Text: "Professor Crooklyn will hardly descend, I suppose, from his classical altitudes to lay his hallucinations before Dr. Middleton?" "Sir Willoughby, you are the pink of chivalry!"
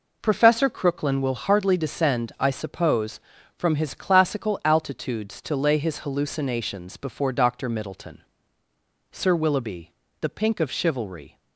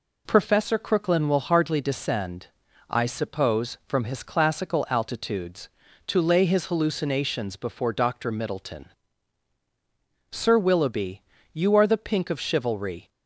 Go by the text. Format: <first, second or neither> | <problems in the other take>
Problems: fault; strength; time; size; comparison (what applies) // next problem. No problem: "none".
second | skips "you are"; at 10.0 s